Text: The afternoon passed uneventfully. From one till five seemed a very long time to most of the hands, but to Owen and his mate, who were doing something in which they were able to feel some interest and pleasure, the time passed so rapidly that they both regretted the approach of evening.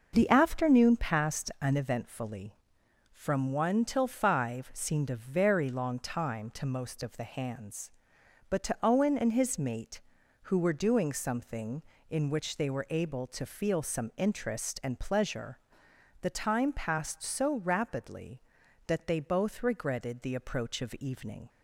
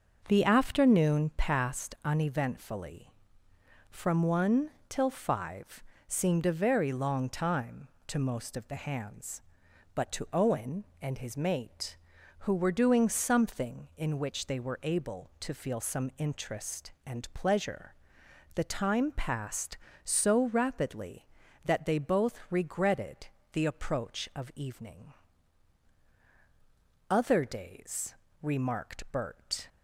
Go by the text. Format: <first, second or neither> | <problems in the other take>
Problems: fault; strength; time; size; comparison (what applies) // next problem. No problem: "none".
first | starts louder than the rest; until 1.2 s; 6.5 dB // pauses between "one" and "till"; slight; at 4.6 s; 0.18 s long // pauses between "five" and "seemed"; slight; at 5.8 s; 0.24 s long // pauses between "regretted" and "the"; slight; at 23.2 s; 0.24 s long // goes on to say "Other days remarked Bert"; strong; from 27.0 s on; 2.5 s long